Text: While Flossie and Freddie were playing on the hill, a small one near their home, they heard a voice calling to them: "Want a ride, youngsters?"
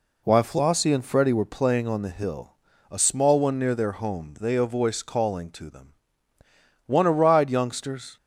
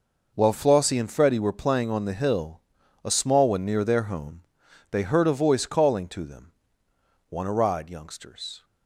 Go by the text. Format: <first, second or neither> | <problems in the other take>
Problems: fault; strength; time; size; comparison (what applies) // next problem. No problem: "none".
second | skips "heard"; at 4.5 s